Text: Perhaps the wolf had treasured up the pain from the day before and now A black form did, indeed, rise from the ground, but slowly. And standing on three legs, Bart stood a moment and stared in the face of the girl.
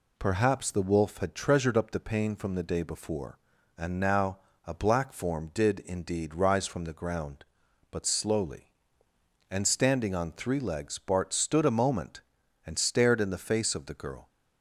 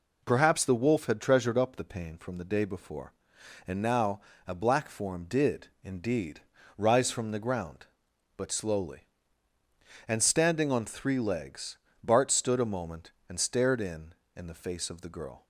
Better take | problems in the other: first | pauses between "now" and "A"; slight; at 4.2 s; 0.26 s long; slight in the first // says "in" twice; at 14.3 s

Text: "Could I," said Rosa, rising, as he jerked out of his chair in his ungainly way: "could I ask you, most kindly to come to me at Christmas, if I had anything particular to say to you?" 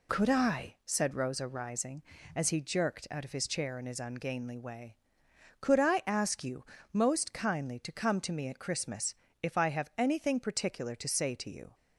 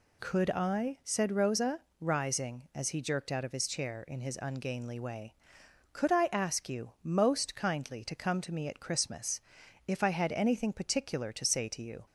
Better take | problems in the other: second | says "have" for "had"; at 9.6 s

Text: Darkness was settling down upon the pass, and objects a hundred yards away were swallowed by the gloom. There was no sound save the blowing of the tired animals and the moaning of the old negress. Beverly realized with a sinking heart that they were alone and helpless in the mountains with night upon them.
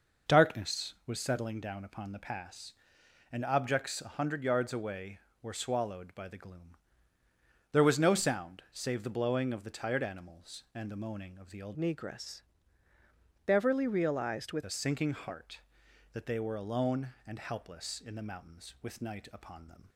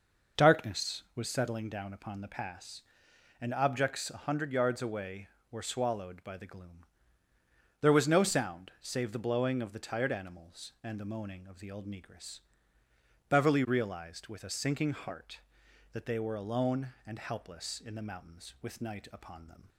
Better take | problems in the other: second | changes voice from "negress" to "with"; from 11.7 to 14.6 s; 2.9 s long

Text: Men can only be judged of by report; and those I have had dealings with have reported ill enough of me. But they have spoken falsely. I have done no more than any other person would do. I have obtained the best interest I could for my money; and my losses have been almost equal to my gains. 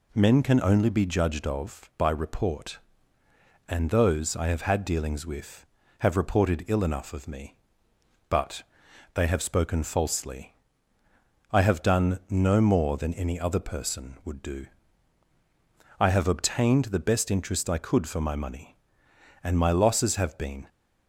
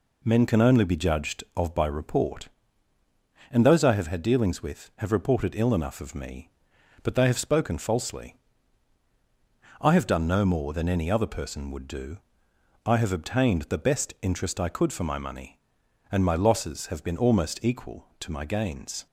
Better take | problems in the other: second | pauses between "But" and "they"; noticeable; at 8.6 s; 0.50 s long // stops before "almost equal to my gains"; at 20.6 s

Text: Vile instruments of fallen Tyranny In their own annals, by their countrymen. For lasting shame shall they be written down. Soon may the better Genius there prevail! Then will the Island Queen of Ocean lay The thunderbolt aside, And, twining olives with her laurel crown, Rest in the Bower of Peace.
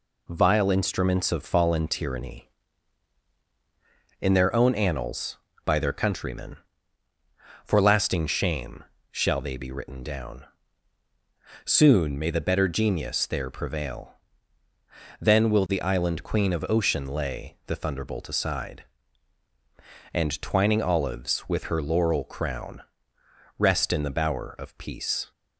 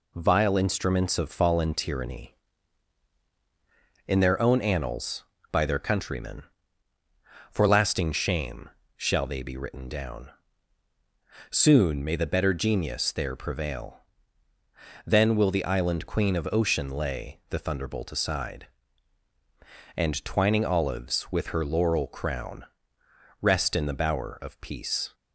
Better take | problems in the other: neither | pauses between "shame" and "shall"; slight; the same in both

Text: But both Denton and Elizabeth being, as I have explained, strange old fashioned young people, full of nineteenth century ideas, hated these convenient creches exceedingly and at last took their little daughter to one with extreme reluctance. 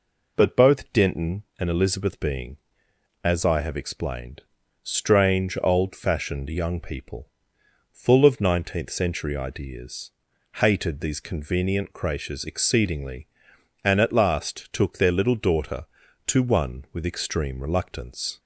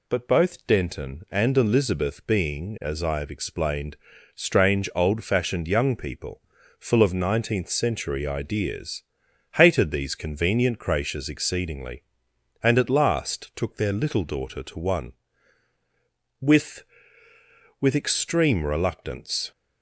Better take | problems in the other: first | says "with" twice; at 17.7 s

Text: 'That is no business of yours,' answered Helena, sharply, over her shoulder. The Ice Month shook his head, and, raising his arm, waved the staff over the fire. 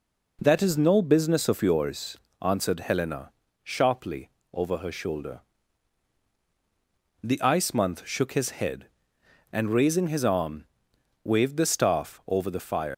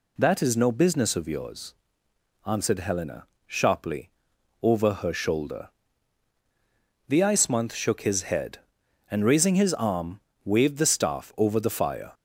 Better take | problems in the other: second | leaves "fire" unfinished; at 12.9 s; 130 ms

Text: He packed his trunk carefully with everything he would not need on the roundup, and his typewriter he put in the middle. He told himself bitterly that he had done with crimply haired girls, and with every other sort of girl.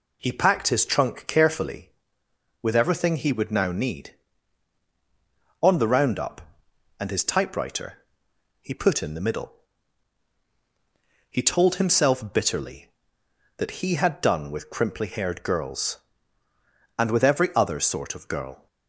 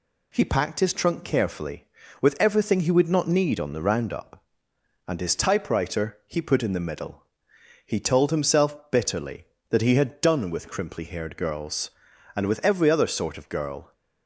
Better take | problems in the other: second | says "now" for "not"; at 3.5 s // pauses between "typewriter" and "he"; noticeable; at 7.9 s; 0.66 s long

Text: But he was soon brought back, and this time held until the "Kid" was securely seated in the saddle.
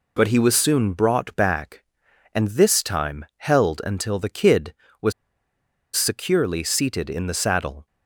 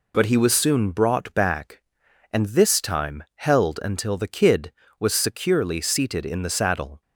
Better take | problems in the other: second | pauses between "was" and "securely"; noticeable; at 5.1 s; 0.83 s long

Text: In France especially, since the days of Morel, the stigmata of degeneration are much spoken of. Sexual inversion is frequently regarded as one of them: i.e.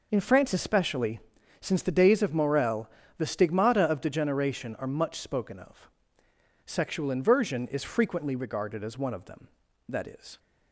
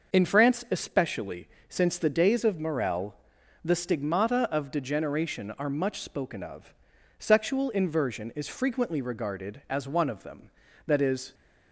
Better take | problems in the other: neither | none

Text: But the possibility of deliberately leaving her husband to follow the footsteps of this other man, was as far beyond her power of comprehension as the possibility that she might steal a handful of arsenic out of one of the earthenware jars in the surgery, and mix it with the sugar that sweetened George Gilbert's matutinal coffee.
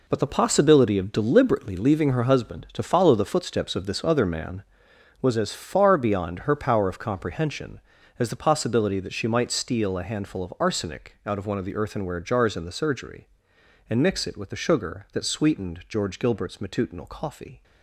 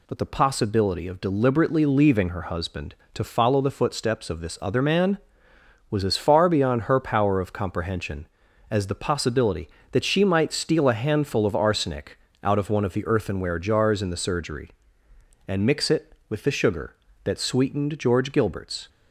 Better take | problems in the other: first | pauses between "arsenic" and "out"; slight; at 12.1 s; 0.24 s long // stops before "matutinal coffee"; at 18.8 s

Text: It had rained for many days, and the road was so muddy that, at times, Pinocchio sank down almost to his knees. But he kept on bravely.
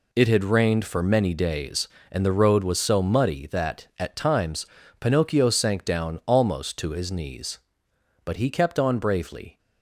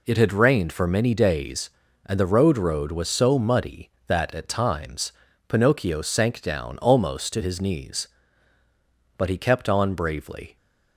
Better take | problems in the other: first | says "road" twice; at 2.5 s

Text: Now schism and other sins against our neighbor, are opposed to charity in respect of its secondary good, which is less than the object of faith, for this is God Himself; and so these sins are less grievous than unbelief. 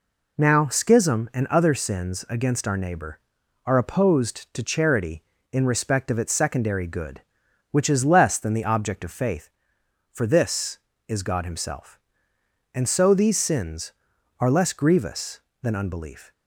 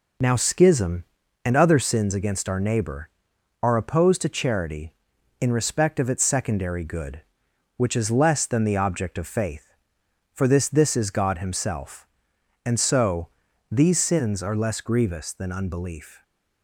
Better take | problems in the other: first | says "this" twice; at 10.6 s // pauses between "so" and "these"; at 13.2 s; 0.40 s long

